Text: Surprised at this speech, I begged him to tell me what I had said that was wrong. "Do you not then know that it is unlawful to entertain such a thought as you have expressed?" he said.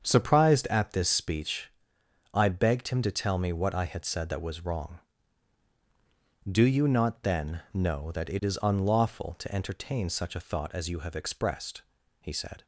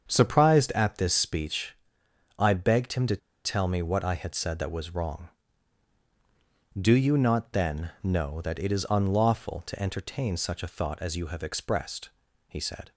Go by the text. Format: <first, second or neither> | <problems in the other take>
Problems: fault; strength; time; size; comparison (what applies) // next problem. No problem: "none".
first | starts louder than the rest; strong; until 1.0 s; 7 dB; strong in the first // pauses between "to" and "tell"; slight; at 3.1 s; 0.29 s long